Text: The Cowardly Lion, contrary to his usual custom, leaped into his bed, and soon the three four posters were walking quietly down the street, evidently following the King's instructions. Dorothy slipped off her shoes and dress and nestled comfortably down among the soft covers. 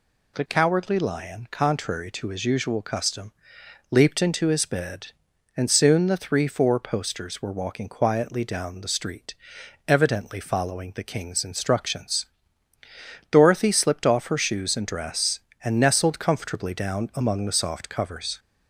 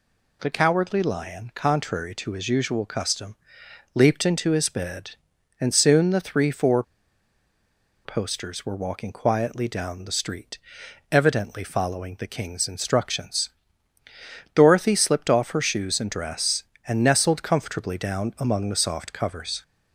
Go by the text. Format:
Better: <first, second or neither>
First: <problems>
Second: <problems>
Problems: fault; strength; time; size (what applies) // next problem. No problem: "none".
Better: first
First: none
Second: pauses between "four" and "posters"; at 6.8 s; 1.2 s long